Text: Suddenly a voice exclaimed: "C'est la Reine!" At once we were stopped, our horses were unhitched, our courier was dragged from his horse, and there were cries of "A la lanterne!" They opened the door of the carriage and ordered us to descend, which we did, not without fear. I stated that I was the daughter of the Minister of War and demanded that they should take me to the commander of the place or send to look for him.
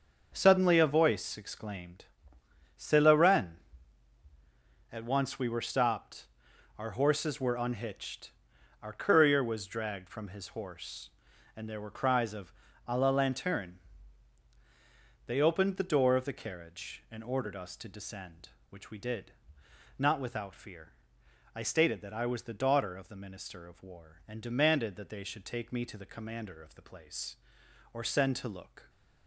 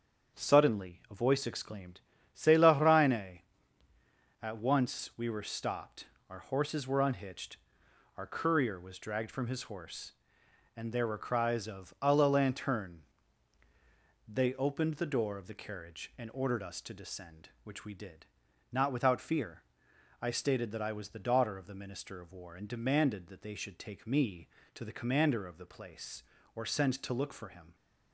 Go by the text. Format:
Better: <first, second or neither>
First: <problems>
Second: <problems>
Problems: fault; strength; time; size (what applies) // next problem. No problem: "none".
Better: second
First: starts louder than the rest; until 1.3 s; 6.5 dB // pauses between "of" and "A"; slight; at 12.5 s; 0.36 s long // stops before "for him"; at 28.8 s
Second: starts louder than the rest; strong; until 1.4 s; 7 dB